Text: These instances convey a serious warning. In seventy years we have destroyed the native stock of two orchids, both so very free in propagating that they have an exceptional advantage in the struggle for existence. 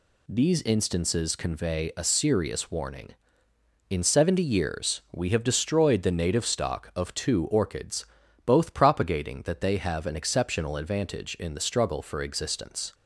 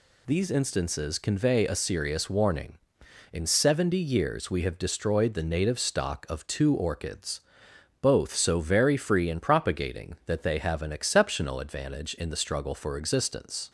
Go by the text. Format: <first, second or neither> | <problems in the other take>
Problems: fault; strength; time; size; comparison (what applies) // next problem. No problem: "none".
second | skips "so very free in"; at 8.7 s